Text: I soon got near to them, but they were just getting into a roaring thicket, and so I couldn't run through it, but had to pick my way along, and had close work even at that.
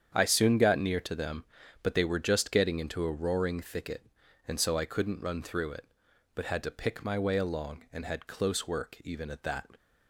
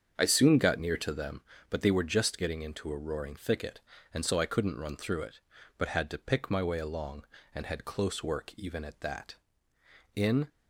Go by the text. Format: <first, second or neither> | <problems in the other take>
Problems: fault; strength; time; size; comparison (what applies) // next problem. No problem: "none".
first | starts louder than the rest; strong; until 1.1 s; 7 dB; strong in the first // goes on to say "In"; slight; from 10.1 s on; 0.32 s long